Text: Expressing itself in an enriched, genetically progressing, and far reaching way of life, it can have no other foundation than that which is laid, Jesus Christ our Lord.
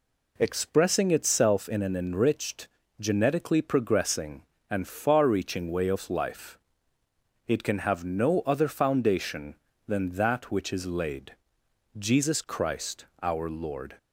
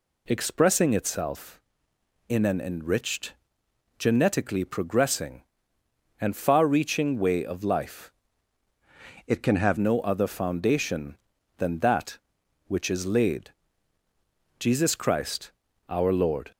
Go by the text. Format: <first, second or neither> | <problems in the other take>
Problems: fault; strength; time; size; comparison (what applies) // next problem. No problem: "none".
first | changes voice from "it" to "have"; from 9.2 to 9.7 s; 0.5 s long // pauses between "Christ" and "our"; slight; at 15.5 s; 0.34 s long; slight in the first